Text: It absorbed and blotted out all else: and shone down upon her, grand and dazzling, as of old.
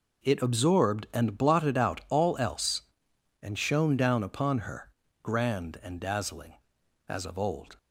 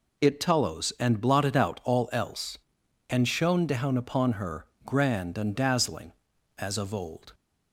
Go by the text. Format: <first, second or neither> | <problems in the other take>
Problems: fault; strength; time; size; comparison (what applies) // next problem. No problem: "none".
first | says "tallows" for "absorbed"; at 0.3 s